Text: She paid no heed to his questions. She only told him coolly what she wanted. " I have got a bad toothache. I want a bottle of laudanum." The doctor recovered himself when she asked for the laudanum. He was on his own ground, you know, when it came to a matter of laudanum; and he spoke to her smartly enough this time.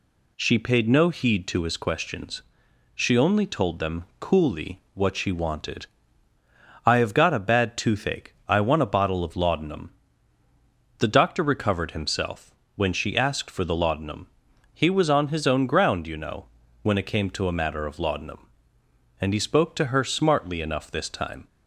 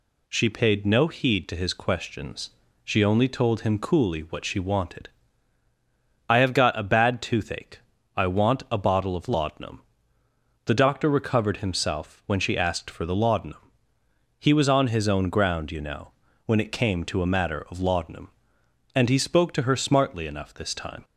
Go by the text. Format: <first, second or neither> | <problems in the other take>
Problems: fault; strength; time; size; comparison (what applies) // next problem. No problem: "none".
second | says "them" for "him"; at 3.7 s // pauses between "himself" and "when"; slight; at 12.5 s; 0.22 s long